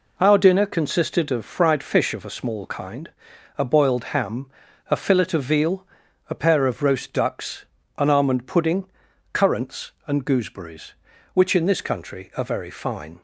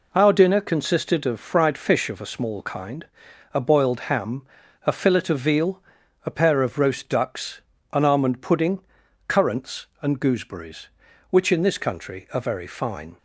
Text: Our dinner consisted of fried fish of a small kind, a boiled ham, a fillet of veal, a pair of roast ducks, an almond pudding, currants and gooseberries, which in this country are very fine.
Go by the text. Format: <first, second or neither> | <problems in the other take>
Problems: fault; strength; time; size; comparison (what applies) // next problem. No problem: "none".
neither | none